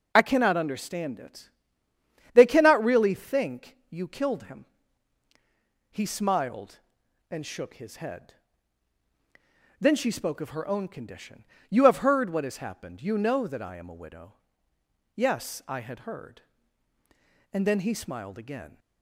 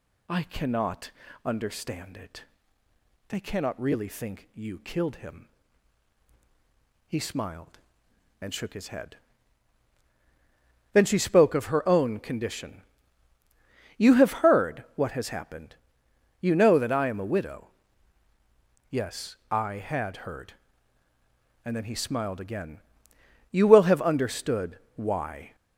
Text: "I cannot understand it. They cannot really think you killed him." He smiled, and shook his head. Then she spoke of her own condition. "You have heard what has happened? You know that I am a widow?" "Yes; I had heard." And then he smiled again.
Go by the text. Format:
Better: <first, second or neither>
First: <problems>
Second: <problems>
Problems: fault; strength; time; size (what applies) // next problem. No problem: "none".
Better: first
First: none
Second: pauses between "cannot" and "understand"; slight; at 1.1 s; 0.34 s long // goes on to say "You will have understood why"; strong; from 23.5 s on; 2.0 s long